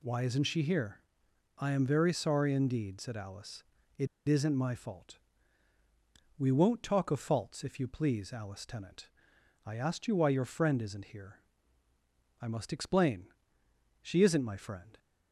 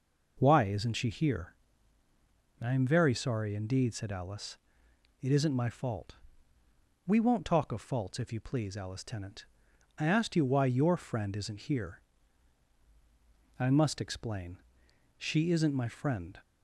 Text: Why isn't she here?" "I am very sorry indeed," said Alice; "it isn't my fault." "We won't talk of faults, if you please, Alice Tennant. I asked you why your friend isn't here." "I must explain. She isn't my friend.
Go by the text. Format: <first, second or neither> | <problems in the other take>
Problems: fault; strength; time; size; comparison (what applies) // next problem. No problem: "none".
second | pauses between "it" and "isn't"; slight; at 4.0 s; 0.21 s long